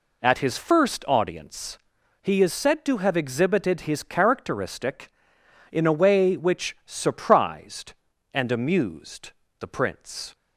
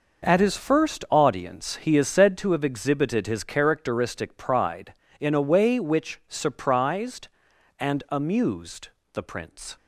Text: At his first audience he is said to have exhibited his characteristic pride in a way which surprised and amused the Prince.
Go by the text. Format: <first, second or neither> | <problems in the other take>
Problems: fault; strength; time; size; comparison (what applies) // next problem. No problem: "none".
second | pauses between "audience" and "he"; at 1.7 s; 0.44 s long // skips "pride"; at 5.3 s // pauses between "amused" and "the"; slight; at 9.2 s; 0.30 s long; slight in the second